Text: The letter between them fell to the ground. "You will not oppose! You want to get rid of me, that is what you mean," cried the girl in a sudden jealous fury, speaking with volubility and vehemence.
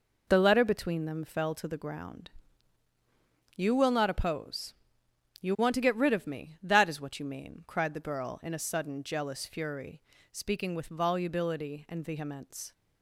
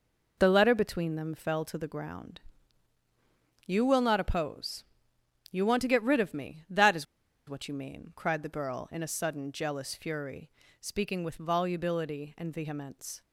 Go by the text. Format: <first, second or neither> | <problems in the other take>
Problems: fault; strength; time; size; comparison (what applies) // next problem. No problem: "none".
first | pauses between "is" and "what"; at 7.0 s; 0.44 s long